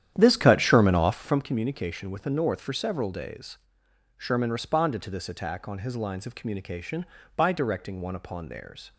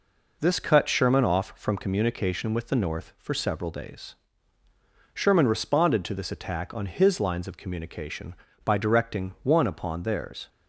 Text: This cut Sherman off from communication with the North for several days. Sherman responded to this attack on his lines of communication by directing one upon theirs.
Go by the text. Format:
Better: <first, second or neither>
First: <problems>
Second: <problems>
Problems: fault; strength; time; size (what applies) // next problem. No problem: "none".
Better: second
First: starts louder than the rest; strong; until 1.5 s; 10.5 dB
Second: none